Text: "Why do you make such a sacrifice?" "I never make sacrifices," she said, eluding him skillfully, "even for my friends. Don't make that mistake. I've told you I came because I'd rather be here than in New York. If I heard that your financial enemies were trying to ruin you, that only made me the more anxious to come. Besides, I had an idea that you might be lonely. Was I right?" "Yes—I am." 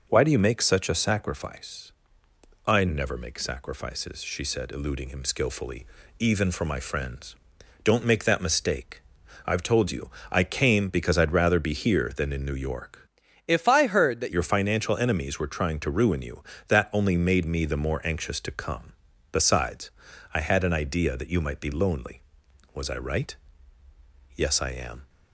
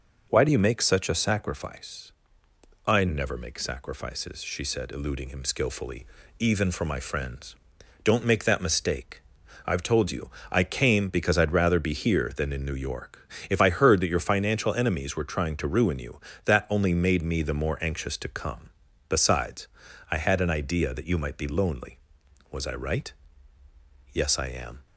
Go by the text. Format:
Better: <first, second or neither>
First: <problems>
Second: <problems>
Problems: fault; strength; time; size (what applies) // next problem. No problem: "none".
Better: second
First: pauses between "you" and "I"; slight; at 10.0 s; 0.22 s long // changes voice from "If" to "that"; from 13.4 to 14.3 s; 0.9 s long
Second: pauses between "you" and "I"; slight; at 10.2 s; 0.22 s long